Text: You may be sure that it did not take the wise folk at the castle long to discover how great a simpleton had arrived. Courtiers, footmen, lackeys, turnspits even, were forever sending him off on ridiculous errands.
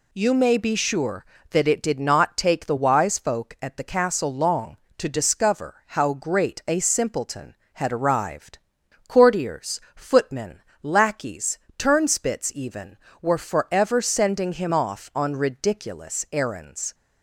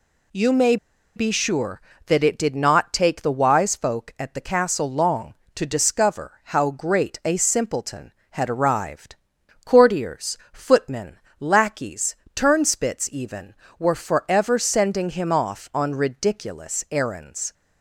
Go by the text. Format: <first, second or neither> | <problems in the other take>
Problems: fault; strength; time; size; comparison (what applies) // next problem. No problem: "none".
first | pauses between "may" and "be"; at 0.7 s; 0.40 s long